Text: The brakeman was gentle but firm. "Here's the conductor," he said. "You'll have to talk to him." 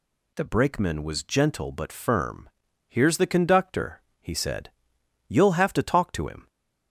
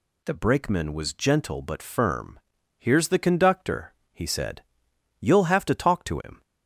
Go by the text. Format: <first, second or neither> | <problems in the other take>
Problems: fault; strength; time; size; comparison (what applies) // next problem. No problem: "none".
neither | none